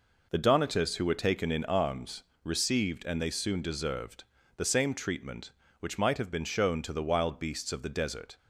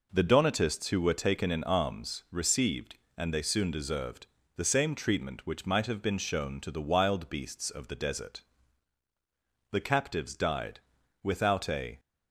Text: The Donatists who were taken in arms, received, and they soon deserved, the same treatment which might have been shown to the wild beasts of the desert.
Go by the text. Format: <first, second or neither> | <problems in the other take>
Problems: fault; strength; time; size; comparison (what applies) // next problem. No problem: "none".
first | goes on to say "The captives died without a"; strong; from 9.7 s on; 2.2 s long